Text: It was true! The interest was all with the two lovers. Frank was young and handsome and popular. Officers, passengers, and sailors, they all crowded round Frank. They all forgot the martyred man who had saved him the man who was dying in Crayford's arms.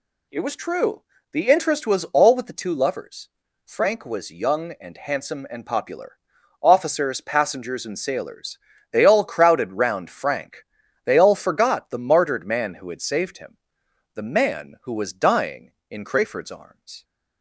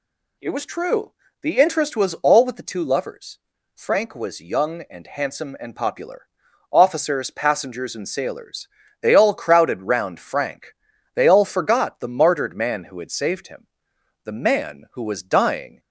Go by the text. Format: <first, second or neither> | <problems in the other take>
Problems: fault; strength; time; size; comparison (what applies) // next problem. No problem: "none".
first | pauses between "him" and "the"; noticeable; at 13.6 s; 0.58 s long; noticeable in the first // stops before "in Crayford's arms"; at 15.7 s